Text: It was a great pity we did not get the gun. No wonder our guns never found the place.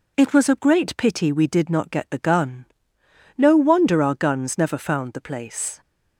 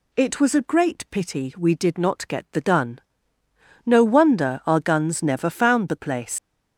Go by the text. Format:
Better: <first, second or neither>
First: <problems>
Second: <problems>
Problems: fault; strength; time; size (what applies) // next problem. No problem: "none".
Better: first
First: none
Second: leaves "place" unfinished; at 6.3 s; 135 ms